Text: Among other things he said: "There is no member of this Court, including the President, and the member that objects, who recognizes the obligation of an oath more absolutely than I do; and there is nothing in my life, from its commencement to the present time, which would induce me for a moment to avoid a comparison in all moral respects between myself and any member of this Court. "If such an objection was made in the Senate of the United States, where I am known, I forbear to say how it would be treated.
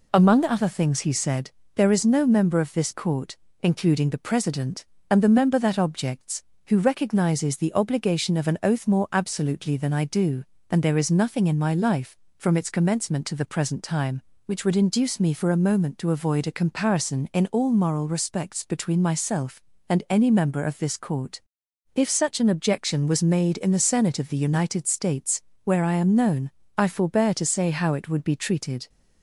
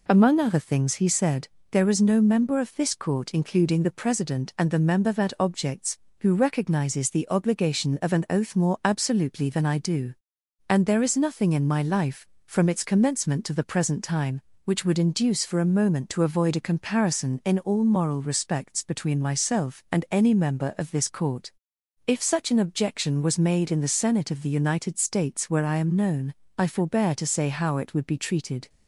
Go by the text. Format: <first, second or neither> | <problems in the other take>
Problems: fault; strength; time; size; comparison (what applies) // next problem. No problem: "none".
first | skips "me"; at 15.4 s